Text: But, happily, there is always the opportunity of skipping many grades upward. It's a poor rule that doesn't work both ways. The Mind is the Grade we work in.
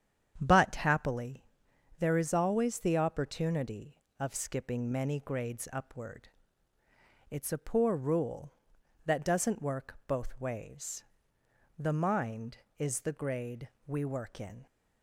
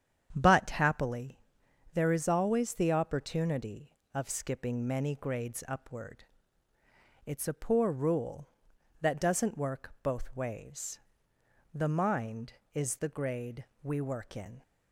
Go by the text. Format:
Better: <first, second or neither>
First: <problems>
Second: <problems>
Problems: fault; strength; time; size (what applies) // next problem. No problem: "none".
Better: neither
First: starts louder than the rest; strong; until 1.4 s; 8.5 dB // pauses between "Grade" and "we"; slight; at 13.6 s; 0.18 s long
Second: starts louder than the rest; strong; until 1.3 s; 8.5 dB // pauses between "Grade" and "we"; slight; at 13.6 s; 0.18 s long